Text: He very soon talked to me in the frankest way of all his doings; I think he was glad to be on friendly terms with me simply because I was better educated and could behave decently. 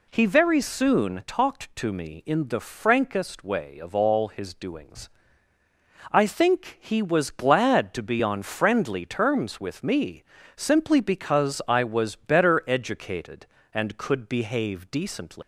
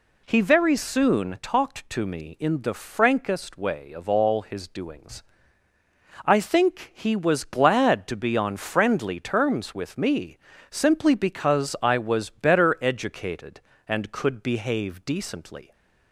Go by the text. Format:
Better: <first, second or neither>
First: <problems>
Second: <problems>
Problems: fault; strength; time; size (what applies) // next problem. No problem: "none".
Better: second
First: pauses between "me" and "simply"; slight; at 10.2 s; 0.32 s long // leaves "decently" unfinished; at 15.4 s; 150 ms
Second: pauses between "me" and "simply"; slight; at 10.3 s; 0.32 s long